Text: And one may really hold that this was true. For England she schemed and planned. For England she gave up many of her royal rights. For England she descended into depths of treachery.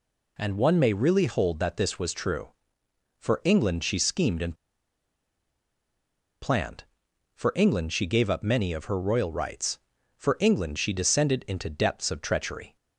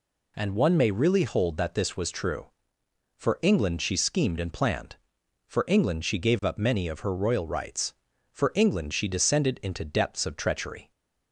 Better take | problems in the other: second | pauses between "and" and "planned"; strong; at 4.5 s; 1.8 s long

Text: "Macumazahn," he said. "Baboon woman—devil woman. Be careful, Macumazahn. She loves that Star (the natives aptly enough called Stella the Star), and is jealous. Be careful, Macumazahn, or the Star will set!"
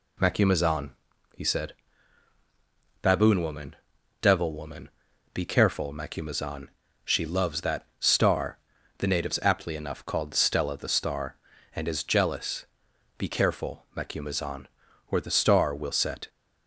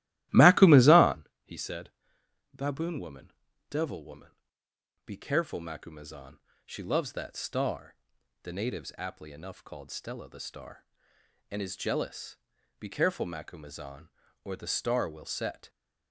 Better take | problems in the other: first | starts louder than the rest; strong; until 1.2 s; 15 dB

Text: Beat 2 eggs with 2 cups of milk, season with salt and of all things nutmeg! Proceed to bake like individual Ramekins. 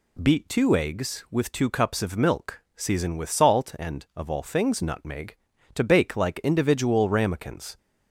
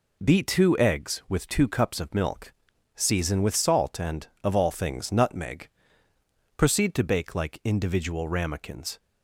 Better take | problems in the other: second | skips "Proceed"; at 5.5 s

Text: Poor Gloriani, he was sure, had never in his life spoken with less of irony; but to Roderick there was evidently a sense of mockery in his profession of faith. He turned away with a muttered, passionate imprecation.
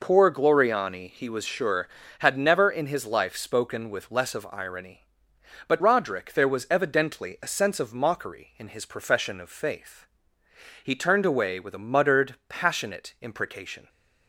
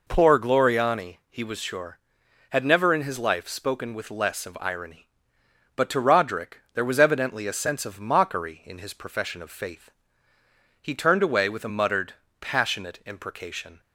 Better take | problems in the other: second | skips "to"; at 5.8 s

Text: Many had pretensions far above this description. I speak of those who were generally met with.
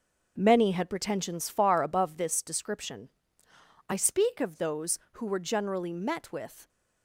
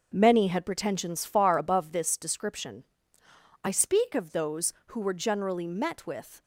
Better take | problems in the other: neither | none

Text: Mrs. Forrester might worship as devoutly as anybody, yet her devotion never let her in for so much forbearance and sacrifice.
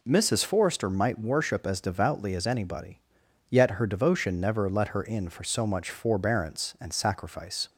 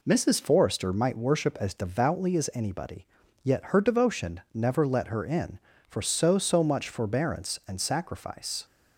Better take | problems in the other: first | says "so" twice; at 6.3 s

